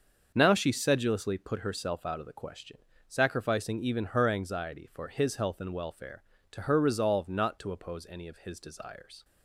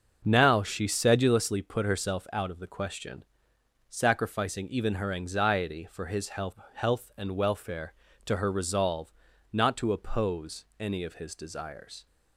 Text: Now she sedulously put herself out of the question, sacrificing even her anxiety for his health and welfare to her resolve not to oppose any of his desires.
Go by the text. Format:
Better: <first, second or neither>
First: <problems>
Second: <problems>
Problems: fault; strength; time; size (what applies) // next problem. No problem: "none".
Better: first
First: starts louder than the rest; until 1.3 s; 6.5 dB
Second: starts louder than the rest; until 1.2 s; 6 dB // says "health" twice; at 6.7 s // pauses between "resolve" and "not"; at 9.1 s; 0.40 s long // pauses between "oppose" and "any"; slight; at 10.6 s; 0.16 s long